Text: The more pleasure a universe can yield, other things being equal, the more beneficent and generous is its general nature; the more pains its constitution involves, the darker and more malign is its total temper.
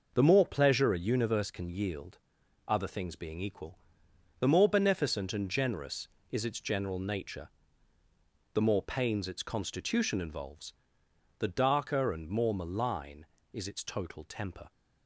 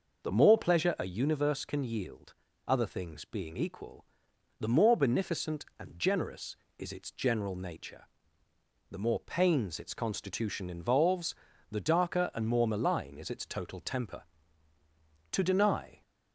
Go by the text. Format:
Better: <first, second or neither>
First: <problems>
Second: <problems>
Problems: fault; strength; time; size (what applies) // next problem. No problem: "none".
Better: first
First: none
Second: goes on to say "To deny"; noticeable; from 15.3 s on; 0.72 s long